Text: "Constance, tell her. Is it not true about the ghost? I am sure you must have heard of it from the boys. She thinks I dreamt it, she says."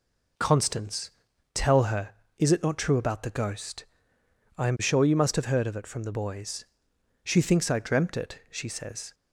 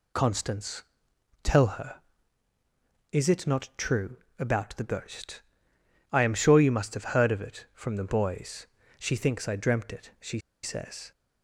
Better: first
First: none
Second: pauses between "true" and "about"; slight; at 4.1 s; 0.22 s long // pauses between "she" and "says"; slight; at 10.3 s; 0.24 s long

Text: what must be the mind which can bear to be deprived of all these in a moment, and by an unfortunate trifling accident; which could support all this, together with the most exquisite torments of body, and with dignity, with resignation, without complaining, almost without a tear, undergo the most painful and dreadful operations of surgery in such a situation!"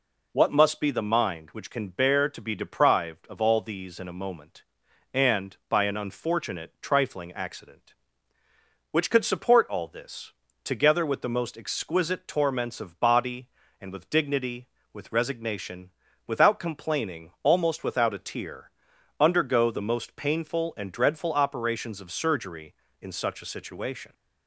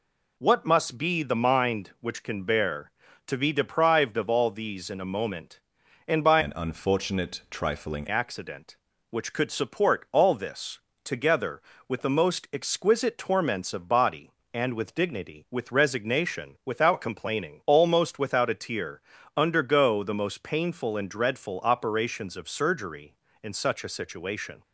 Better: first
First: none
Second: changes voice from "an" to "trifling"; from 6.4 to 8.0 s; 1.6 s long

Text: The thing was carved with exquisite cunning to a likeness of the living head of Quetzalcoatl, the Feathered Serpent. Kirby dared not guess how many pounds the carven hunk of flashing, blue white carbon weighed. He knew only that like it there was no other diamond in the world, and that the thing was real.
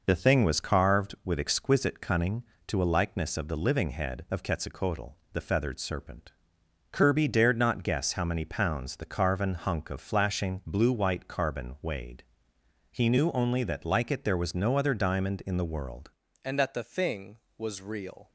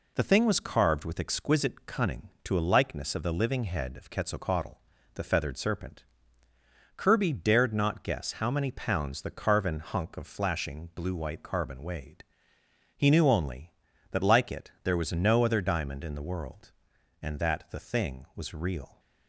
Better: second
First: changes voice at "and"; from 16.4 s on; 1.8 s long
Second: none

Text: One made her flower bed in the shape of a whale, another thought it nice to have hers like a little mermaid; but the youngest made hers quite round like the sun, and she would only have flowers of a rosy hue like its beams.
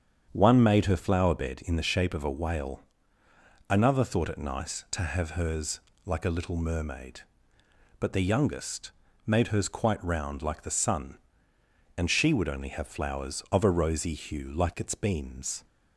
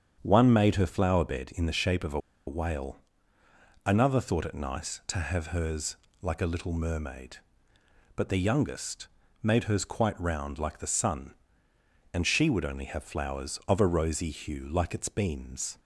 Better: first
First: starts louder than the rest; strong; until 1.3 s; 8 dB // pauses between "hers" and "like"; slight; at 5.7 s; 0.26 s long // pauses between "youngest" and "made"; slight; at 8.9 s; 0.34 s long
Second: starts louder than the rest; strong; until 1.2 s; 8 dB // pauses between "a" and "whale"; slight; at 2.1 s; 0.27 s long // pauses between "hers" and "like"; slight; at 5.9 s; 0.26 s long // pauses between "youngest" and "made"; slight; at 9.0 s; 0.34 s long

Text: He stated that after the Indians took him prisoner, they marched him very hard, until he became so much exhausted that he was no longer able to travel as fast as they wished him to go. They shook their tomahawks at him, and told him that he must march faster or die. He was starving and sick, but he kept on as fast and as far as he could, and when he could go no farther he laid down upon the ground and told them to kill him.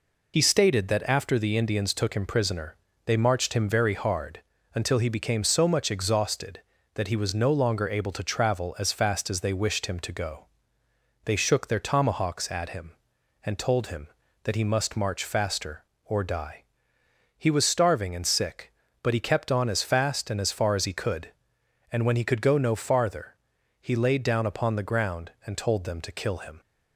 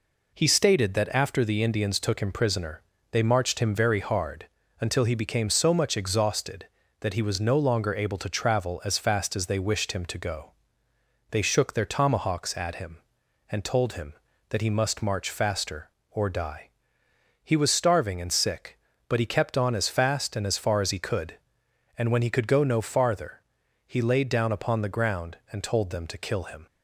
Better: second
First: loses the start of "He"; at 0.3 s; 60 ms // pauses between "farther" and "he"; noticeable; at 23.3 s; 0.46 s long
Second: pauses between "farther" and "he"; noticeable; at 23.3 s; 0.46 s long

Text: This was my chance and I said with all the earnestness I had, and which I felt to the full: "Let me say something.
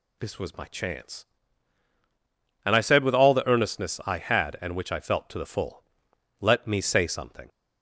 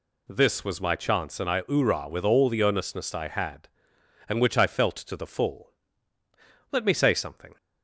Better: first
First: none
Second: says "oorah" for "said"; at 1.6 s

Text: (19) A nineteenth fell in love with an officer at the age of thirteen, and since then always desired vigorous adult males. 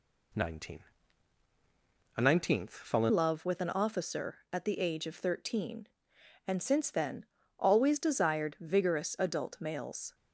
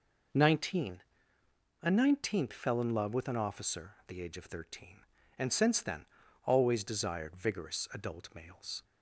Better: second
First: changes voice at "love"; from 3.1 s on; 7.0 s long // pauses between "then" and "always"; slight; at 7.2 s; 0.32 s long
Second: pauses between "then" and "always"; at 6.0 s; 0.40 s long

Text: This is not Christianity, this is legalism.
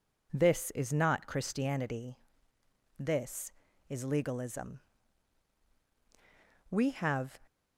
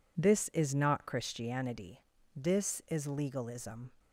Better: second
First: goes on to say "We have"; noticeable; from 6.7 s on; 0.70 s long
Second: none

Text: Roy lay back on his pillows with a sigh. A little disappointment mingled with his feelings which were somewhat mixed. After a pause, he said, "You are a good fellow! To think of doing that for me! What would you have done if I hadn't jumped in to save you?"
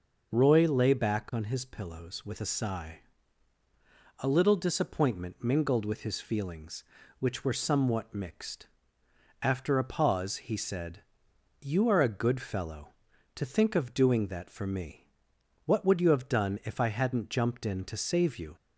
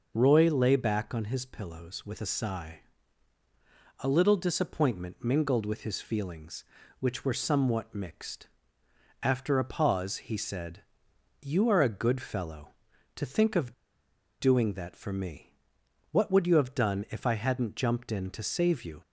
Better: first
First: none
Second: pauses between "of" and "doing"; noticeable; at 13.7 s; 0.66 s long

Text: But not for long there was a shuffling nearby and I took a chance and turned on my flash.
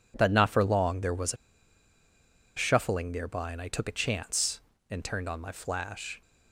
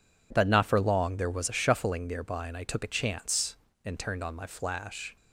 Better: second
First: pauses between "a" and "shuffling"; at 1.3 s; 1.2 s long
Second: none

